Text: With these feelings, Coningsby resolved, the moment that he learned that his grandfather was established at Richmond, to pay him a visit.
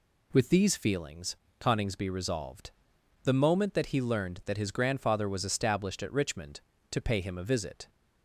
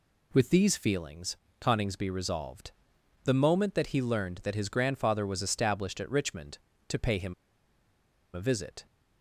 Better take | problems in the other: first | pauses between "him" and "a"; at 7.3 s; 1.0 s long

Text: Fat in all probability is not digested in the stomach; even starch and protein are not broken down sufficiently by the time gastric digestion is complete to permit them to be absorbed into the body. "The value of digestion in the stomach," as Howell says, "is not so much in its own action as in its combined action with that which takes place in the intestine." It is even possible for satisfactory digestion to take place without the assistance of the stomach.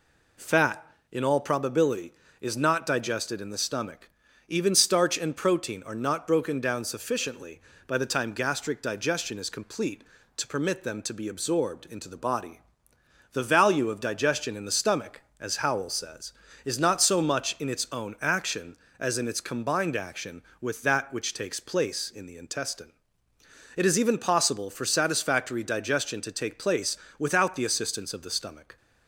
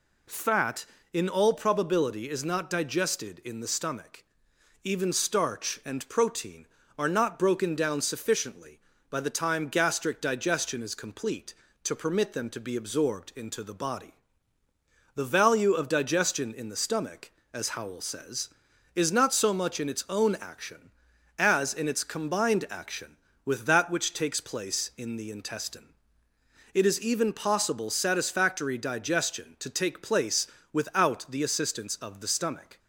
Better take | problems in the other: first | skips "for"; at 27.8 s // pauses between "place" and "without"; slight; at 30.4 s; 0.24 s long; slight in the first

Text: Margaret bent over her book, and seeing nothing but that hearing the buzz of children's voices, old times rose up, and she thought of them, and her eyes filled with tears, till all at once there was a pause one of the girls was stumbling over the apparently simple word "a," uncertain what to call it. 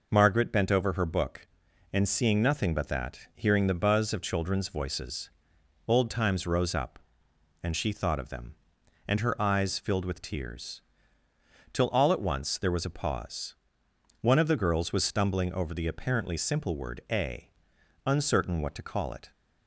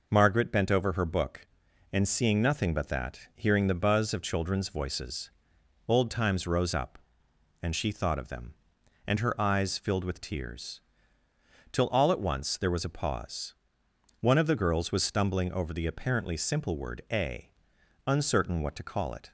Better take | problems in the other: neither | pauses between "pause" and "one"; noticeable; the same in both

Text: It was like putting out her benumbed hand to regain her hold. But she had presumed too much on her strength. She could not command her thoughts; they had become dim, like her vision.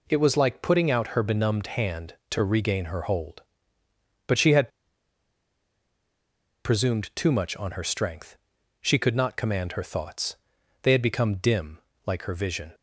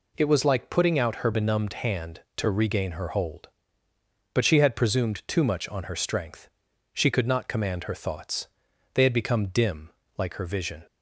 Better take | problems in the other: second | pauses between "had" and "presumed"; strong; at 4.6 s; 1.9 s long

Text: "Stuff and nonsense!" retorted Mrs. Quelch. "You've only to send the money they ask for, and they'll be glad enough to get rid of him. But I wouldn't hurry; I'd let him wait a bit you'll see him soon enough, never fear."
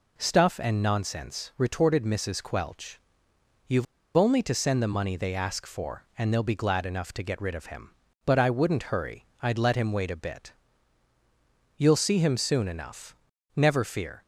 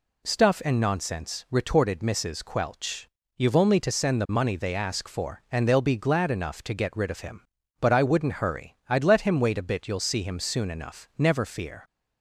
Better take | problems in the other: second | pauses between "You've" and "only"; slight; at 3.8 s; 0.32 s long // pauses between "bit" and "you'll"; at 10.5 s; 1.2 s long

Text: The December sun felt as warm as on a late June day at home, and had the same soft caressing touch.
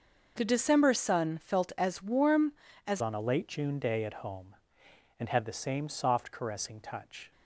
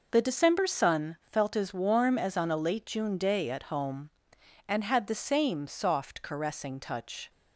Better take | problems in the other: second | starts louder than the rest; noticeable; until 1.3 s; 6 dB // changes voice at "on"; from 3.0 s on; 4.3 s long

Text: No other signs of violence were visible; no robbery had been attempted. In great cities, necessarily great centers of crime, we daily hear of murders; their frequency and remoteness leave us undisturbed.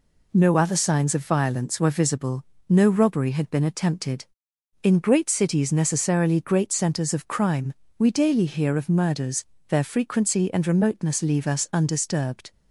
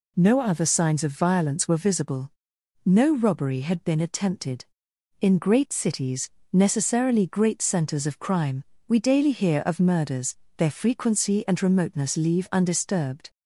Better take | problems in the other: first | skips "us"; at 12.4 s

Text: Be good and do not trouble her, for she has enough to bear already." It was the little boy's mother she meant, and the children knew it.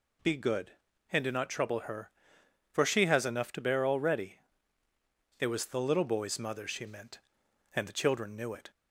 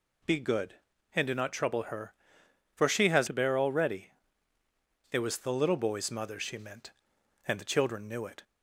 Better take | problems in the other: first | skips "enough"; at 3.2 s

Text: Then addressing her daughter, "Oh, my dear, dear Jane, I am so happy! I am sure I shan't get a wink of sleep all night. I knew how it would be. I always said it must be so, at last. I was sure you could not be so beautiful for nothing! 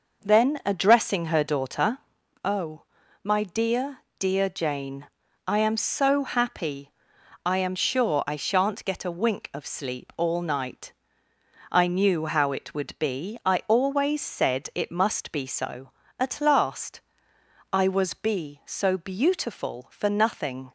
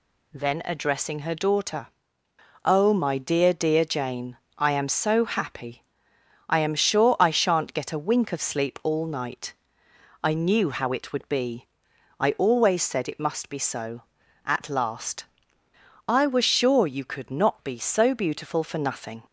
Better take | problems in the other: second | skips "sure you could not"; at 18.1 s

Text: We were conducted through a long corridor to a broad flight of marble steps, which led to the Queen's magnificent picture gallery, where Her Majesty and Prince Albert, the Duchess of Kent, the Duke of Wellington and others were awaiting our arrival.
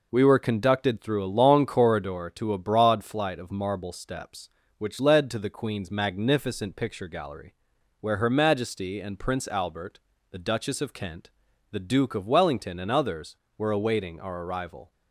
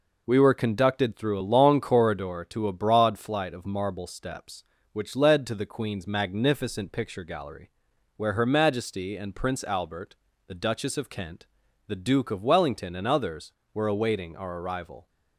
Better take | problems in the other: neither | none

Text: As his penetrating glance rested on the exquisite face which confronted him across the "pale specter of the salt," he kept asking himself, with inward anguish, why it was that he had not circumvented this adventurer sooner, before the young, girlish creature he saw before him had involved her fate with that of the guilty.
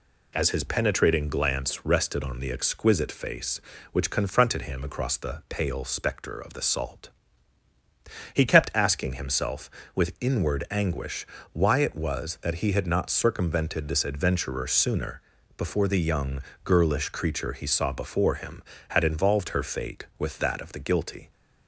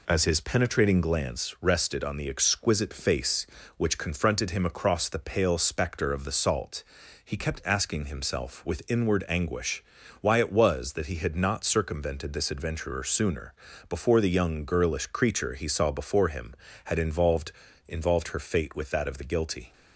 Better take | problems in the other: first | says "involved" twice; at 17.8 s

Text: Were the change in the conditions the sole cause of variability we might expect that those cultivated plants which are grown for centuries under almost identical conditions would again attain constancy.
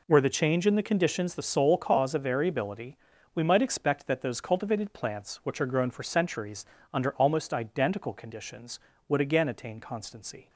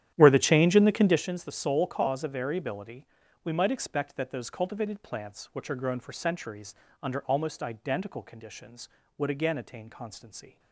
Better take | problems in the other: first | starts louder than the rest; strong; until 1.2 s; 11 dB // pauses between "variability" and "we"; at 3.0 s; 0.38 s long; also in the first // pauses between "centuries" and "under"; slight; at 6.7 s; 0.26 s long; slight in the first

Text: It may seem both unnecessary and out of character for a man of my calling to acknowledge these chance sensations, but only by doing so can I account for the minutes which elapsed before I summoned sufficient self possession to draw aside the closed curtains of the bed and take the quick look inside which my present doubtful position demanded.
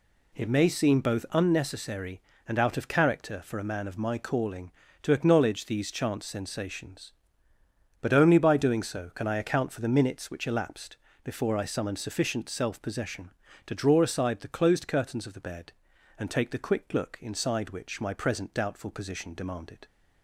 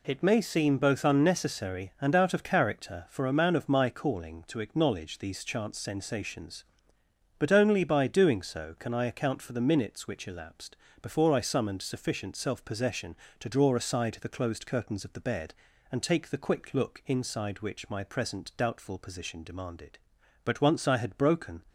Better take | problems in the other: first | pauses between "elapsed" and "before"; slight; at 10.7 s; 0.26 s long; slight in the first // goes on to say "But once I had broken"; noticeable; from 20.4 s on; 1.2 s long

